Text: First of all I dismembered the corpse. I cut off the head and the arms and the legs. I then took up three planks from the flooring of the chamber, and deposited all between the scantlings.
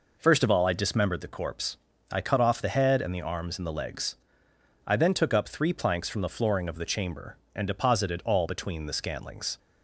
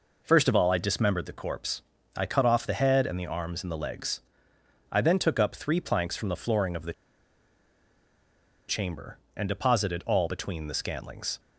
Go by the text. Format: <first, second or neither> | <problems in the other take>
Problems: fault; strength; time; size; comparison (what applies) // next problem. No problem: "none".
first | pauses between "the" and "chamber"; strong; at 6.9 s; 1.7 s long